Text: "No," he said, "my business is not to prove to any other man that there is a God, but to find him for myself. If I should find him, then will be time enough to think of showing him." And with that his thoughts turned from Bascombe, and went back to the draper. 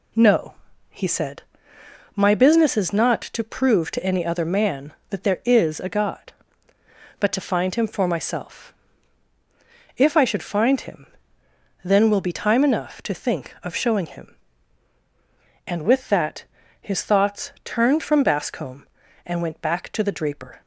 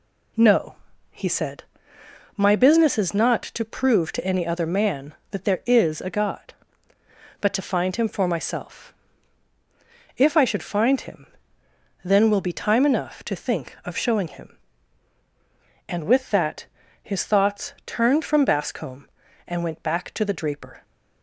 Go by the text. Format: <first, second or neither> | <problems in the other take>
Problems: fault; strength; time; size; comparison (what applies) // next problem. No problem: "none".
neither | pauses between "that" and "his"; slight; the same in both